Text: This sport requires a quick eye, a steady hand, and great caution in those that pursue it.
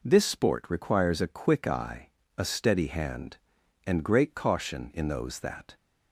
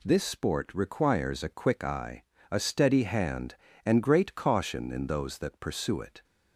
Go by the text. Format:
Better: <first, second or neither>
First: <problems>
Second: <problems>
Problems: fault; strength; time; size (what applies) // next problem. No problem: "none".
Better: second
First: stops before "pursue it"; at 5.7 s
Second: none